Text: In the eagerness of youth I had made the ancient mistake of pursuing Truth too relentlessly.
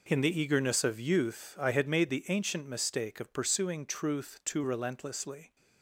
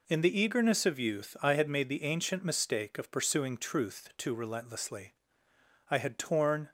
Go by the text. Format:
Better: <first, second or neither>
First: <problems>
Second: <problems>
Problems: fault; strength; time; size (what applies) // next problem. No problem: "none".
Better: first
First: none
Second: goes on to say "I had torn"; noticeable; from 5.8 s on; 0.80 s long